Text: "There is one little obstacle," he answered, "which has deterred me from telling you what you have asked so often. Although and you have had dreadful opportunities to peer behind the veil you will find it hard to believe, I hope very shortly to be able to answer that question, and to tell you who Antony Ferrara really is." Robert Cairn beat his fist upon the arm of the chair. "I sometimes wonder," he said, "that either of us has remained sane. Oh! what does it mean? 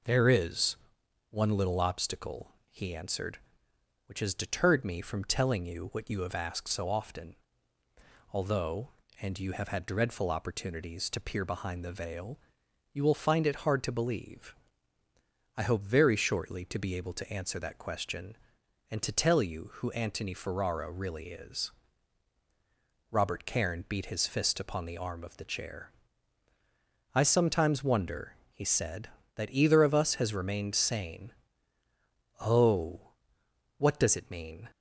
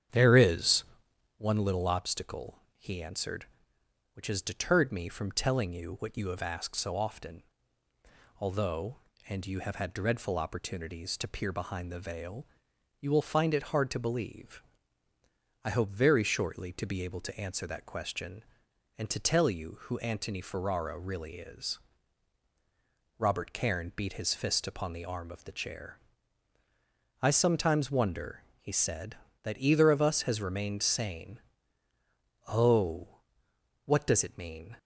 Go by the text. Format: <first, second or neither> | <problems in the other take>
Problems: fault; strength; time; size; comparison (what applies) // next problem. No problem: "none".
first | starts louder than the rest; strong; until 1.5 s; 8.5 dB // pauses between "is" and "one"; noticeable; at 0.8 s; 0.54 s long; noticeable in the first // pauses between "veil" and "you"; noticeable; at 12.4 s; 0.54 s long; noticeable in the first